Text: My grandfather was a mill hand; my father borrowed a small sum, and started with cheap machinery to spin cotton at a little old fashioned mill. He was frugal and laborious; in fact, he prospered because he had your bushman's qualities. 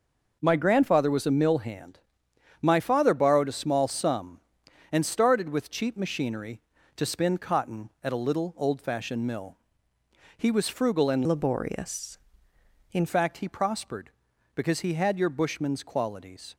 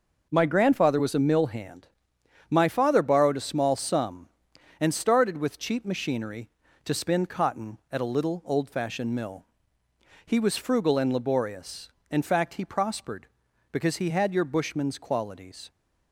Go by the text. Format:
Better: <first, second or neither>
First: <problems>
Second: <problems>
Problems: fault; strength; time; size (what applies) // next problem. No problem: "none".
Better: second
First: changes voice from "laborious" to "in"; from 11.2 to 13.0 s; 1.8 s long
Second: none